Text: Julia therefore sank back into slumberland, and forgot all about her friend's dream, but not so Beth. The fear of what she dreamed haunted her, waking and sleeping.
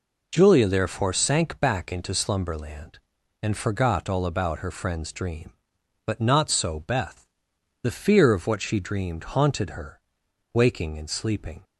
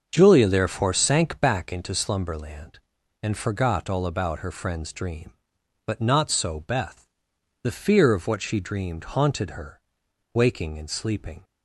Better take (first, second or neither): first